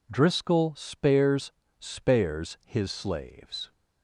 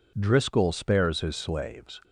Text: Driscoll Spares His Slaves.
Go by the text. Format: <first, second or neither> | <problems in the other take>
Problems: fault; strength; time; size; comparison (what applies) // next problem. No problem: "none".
second | says "Spares" twice; at 1.7 s